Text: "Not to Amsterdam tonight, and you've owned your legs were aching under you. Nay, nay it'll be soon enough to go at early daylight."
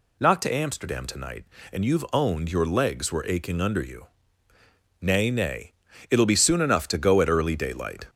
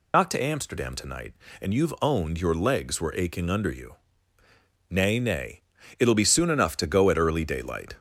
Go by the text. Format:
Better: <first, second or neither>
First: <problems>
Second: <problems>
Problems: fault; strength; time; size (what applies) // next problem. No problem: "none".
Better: first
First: pauses between "nay" and "it'll"; at 5.7 s; 0.38 s long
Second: loses the start of "Not"; at 0.1 s; 60 ms // pauses between "nay" and "it'll"; at 5.6 s; 0.38 s long